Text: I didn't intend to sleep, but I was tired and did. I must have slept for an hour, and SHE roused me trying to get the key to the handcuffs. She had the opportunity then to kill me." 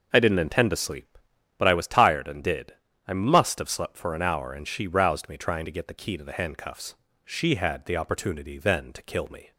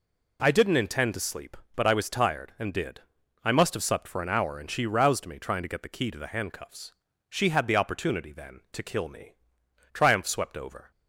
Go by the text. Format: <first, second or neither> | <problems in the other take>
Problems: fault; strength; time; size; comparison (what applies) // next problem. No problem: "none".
first | goes on to say "Triumph swept over"; noticeable; from 9.9 s on; 0.99 s long